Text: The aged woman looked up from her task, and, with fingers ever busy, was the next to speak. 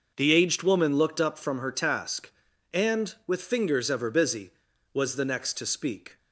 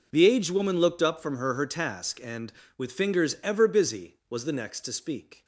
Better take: first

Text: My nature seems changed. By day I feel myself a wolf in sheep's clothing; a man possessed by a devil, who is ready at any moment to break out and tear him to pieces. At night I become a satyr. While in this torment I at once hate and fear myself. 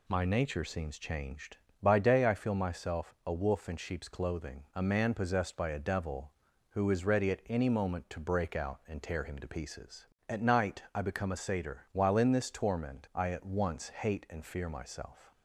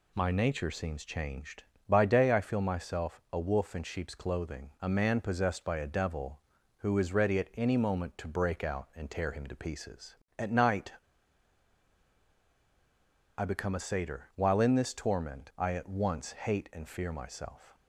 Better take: first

